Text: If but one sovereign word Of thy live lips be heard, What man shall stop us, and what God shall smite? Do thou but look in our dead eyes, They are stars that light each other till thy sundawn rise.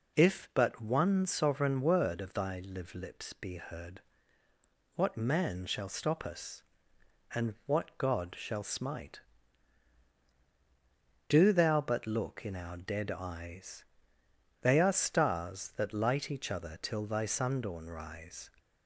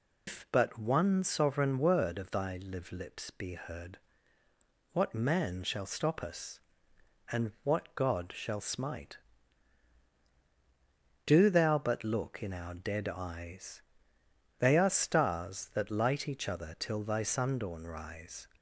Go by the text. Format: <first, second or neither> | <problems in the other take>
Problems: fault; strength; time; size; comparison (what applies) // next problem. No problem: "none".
first | loses the start of "If"; at 0.2 s; 145 ms